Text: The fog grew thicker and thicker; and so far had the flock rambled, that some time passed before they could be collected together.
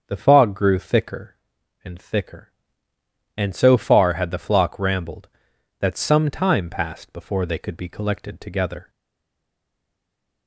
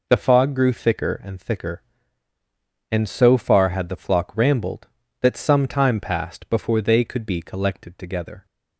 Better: second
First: starts louder than the rest; until 1.1 s; 6.5 dB // stays silent after the last word; noticeable; from 8.8 s on; 1.6 s long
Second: none

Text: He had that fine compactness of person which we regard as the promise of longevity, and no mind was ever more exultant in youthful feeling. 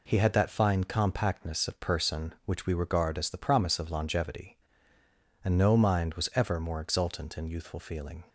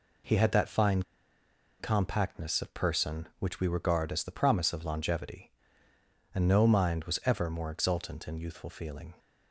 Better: first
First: none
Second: pauses between "fine" and "compactness"; noticeable; at 1.0 s; 0.76 s long

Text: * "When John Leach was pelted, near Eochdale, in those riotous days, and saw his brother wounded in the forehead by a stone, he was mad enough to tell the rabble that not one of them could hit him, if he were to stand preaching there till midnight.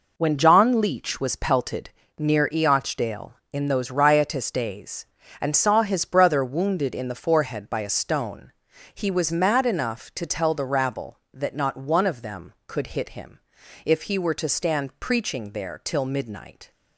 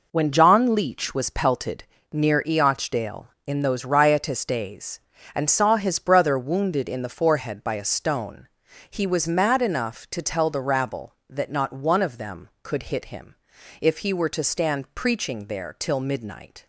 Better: neither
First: none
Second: none

